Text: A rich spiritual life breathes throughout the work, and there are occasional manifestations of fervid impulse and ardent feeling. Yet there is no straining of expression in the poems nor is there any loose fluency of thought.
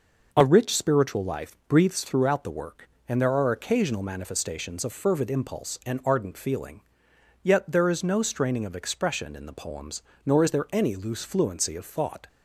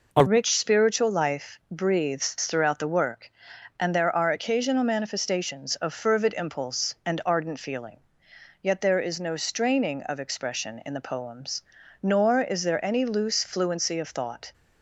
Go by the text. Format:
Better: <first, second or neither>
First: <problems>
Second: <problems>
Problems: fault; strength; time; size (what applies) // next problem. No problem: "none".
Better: first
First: pauses between "poems" and "nor"; slight; at 10.0 s; 0.22 s long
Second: changes voice at "rich"; from 0.2 s on; 14.3 s long // pauses between "poems" and "nor"; at 11.6 s; 0.40 s long